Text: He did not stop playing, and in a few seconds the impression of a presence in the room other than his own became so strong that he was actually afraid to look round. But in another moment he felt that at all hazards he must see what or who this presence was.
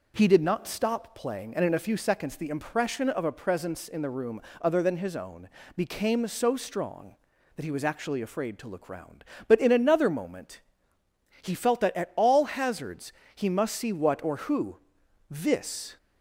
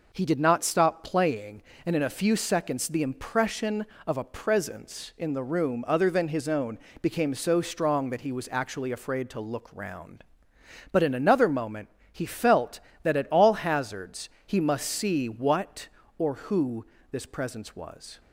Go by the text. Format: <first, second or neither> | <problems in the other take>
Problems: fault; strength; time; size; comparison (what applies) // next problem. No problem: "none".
second | pauses between "room" and "other"; slight; at 4.4 s; 0.20 s long // pauses between "own" and "became"; slight; at 5.4 s; 0.26 s long; slight in the second // pauses between "moment" and "he"; noticeable; at 10.6 s; 0.80 s long; slight in the second // pauses between "hazards" and "he"; slight; at 13.1 s; 0.24 s long; slight in the second // pauses between "who" and "this"; noticeable; at 14.7 s; 0.52 s long; slight in the second // stops before "presence was"; at 15.9 s